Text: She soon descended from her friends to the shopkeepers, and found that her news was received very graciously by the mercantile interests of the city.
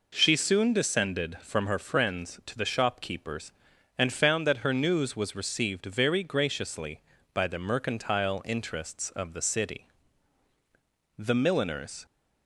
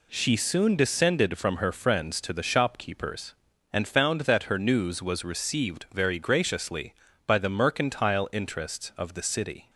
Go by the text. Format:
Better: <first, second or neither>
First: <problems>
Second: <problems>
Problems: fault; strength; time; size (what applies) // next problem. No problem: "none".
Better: second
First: goes on to say "The milliners"; noticeable; from 11.1 s on; 0.88 s long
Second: none